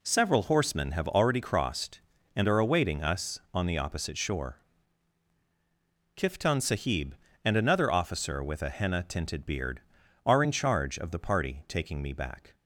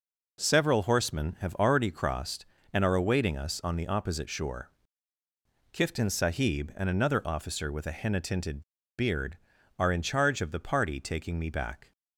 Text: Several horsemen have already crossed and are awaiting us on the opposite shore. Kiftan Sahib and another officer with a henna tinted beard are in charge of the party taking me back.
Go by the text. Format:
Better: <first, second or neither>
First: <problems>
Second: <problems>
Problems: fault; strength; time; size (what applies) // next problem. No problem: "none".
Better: first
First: none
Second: pauses between "tinted" and "beard"; at 8.6 s; 0.37 s long